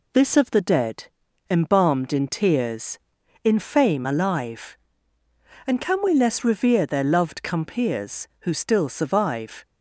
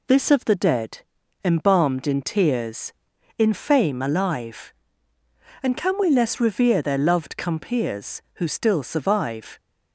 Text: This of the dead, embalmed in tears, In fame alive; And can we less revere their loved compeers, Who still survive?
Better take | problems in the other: neither | none

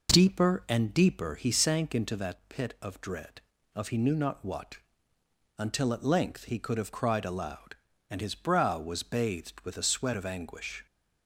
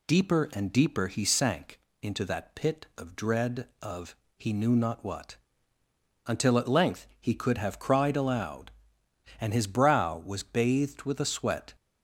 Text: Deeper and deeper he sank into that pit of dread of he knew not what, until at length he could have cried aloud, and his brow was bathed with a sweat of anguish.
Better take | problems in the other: first | pauses between "sank" and "into"; slight; at 1.7 s; 0.22 s long // pauses between "of" and "he"; slight; at 4.1 s; 0.20 s long // stops before "of anguish"; at 11.7 s

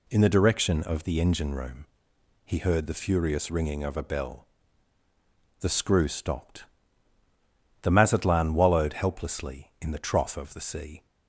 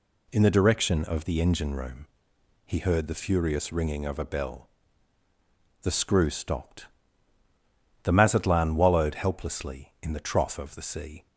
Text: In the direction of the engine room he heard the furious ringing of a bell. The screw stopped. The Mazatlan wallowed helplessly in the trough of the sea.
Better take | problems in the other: neither | pauses between "room" and "he"; noticeable; the same in both

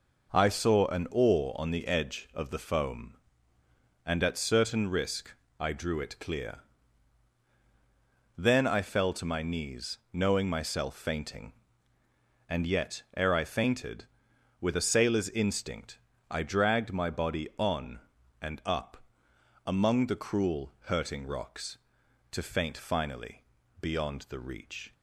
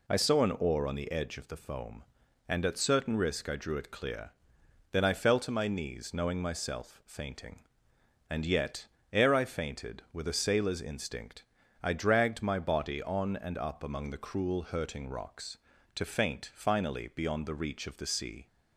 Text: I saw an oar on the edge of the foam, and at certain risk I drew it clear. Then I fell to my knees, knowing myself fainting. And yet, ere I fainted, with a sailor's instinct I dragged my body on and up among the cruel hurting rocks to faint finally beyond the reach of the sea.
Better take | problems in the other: second | pauses between "risk" and "I"; slight; at 5.3 s; 0.28 s long // pauses between "instinct" and "I"; slight; at 15.9 s; 0.32 s long; also in the second // pauses between "up" and "among"; noticeable; at 18.9 s; 0.68 s long // pauses between "finally" and "beyond"; at 23.4 s; 0.38 s long // stops before "of the sea"; at 24.9 s

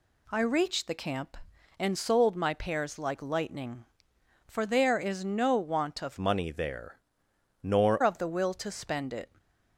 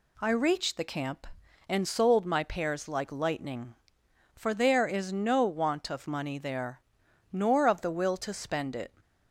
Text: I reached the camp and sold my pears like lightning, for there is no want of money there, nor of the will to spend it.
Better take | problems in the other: second | changes voice from "money" to "nor"; from 6.1 to 8.0 s; 1.9 s long

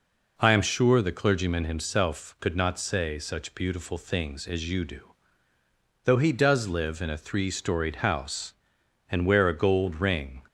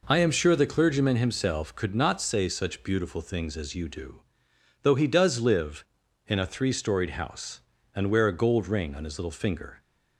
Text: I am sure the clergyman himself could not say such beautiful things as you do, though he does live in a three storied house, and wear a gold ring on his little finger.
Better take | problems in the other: second | stops before "on his little finger"; at 10.4 s

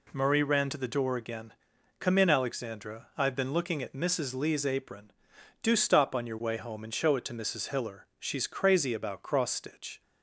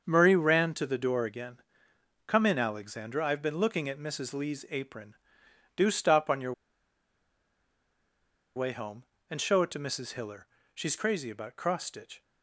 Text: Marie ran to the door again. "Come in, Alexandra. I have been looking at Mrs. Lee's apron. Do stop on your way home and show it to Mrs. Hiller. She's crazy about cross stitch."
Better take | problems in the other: first | starts louder than the rest; until 1.0 s; 6.5 dB // pauses between "your" and "way"; strong; at 6.5 s; 2.0 s long

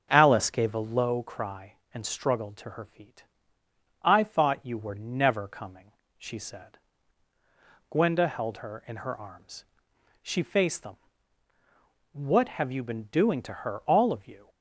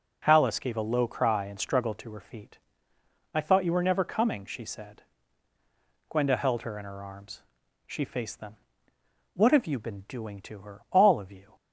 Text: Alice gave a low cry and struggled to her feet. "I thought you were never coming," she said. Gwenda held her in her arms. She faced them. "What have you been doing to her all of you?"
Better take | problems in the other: second | starts louder than the rest; until 1.1 s; 6.5 dB

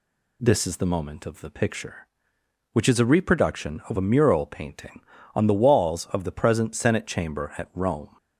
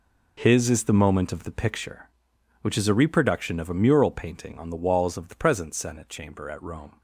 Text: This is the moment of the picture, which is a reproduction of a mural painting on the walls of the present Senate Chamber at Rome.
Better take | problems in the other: first | says "His" for "This"; at 0.3 s

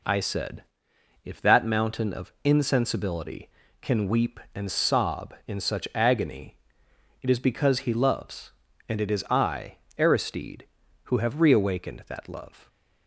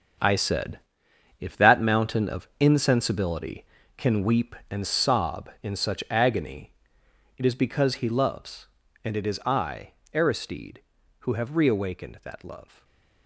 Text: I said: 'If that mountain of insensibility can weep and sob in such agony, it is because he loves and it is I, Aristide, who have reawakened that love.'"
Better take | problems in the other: first | gets quieter; strong; throughout; 10 dB // stays silent after the last word; slight; from 12.6 s on; 0.6 s long

